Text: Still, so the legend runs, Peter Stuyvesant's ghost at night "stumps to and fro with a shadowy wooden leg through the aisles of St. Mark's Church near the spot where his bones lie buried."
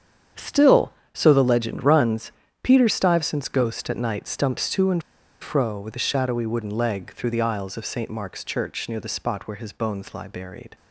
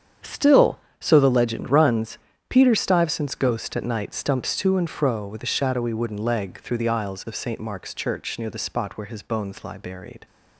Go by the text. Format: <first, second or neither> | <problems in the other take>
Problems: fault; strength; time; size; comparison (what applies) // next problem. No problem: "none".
second | starts louder than the rest; strong; until 1.5 s; 8 dB; strong in the second // pauses between "and" and "fro"; at 5.0 s; 0.39 s long